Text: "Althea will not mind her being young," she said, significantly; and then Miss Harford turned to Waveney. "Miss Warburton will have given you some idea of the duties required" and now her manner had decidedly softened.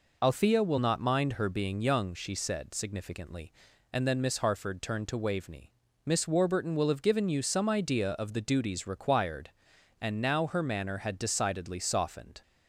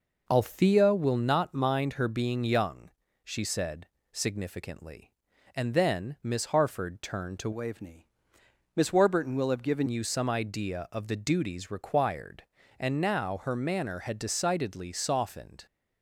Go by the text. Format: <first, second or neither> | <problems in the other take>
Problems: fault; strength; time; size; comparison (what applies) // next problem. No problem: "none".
first | changes voice from "Waveney" to "given"; from 7.5 to 9.8 s; 2.3 s long